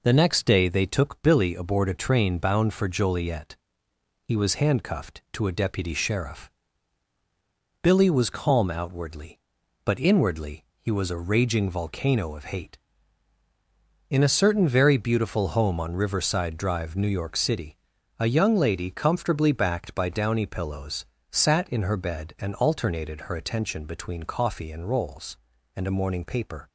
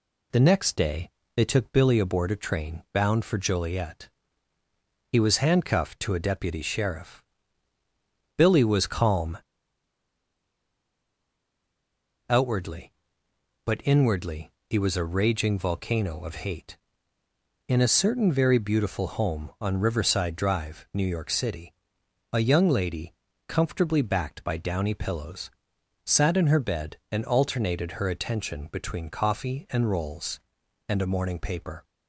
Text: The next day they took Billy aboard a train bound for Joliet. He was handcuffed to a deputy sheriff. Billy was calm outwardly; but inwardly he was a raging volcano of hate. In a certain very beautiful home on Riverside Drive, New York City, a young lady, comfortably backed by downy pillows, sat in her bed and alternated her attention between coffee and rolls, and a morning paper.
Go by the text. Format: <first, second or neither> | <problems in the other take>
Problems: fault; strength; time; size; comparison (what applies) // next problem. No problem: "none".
first | pauses between "day" and "they"; slight; at 1.0 s; 0.26 s long // pauses between "calm" and "outwardly"; strong; at 9.3 s; 2.9 s long // pauses between "inwardly" and "he"; slight; at 14.4 s; 0.20 s long; slight in the first